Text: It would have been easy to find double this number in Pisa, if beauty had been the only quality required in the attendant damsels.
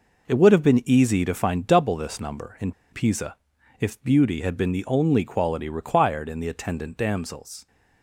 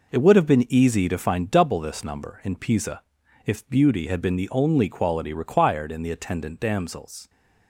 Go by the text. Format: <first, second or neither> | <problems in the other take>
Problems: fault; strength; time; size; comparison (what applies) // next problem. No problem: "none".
second | pauses between "in" and "Pisa"; slight; at 2.7 s; 0.20 s long